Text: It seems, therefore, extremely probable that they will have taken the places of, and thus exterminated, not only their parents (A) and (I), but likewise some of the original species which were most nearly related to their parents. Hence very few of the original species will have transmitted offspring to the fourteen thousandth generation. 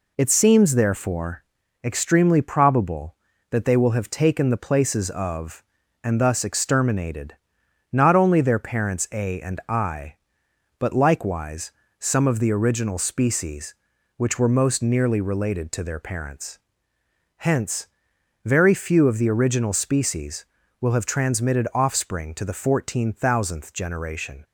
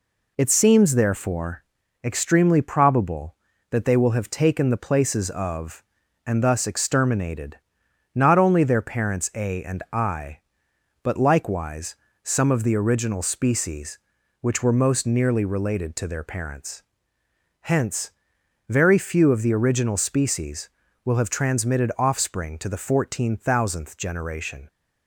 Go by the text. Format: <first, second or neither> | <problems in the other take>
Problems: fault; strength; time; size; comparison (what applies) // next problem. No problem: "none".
neither | pauses between "likewise" and "some"; slight; the same in both // pauses between "Hence" and "very"; noticeable; the same in both